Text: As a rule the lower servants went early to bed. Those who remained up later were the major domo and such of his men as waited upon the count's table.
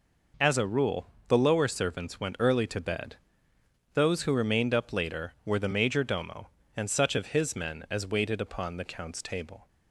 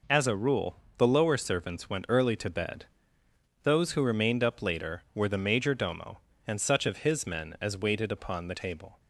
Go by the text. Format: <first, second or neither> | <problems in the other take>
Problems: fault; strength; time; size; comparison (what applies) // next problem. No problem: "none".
first | pauses between "rule" and "the"; slight; at 0.7 s; 0.22 s long; slight in the first // skips "count's"; at 8.5 s